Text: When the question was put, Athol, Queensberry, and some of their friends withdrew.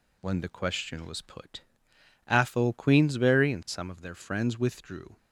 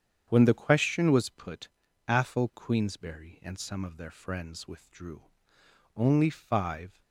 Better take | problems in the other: first | starts louder than the rest; strong; until 1.3 s; 8 dB // goes on to say "Only five"; noticeable; from 5.9 s on; 1.0 s long

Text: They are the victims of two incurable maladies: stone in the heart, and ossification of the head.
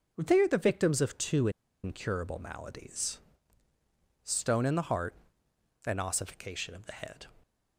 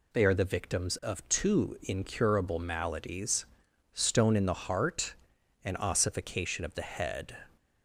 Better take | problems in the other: second | pauses between "two" and "incurable"; slight; at 1.4 s; 0.34 s long

